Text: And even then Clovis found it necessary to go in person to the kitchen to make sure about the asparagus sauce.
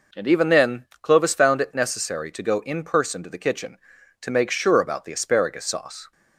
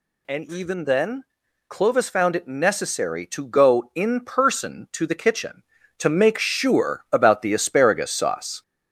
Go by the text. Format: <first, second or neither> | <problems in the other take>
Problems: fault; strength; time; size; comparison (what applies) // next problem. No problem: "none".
first | gets louder; throughout; 4 dB // pauses between "then" and "Clovis"; noticeable; at 1.2 s; 0.46 s long; slight in the first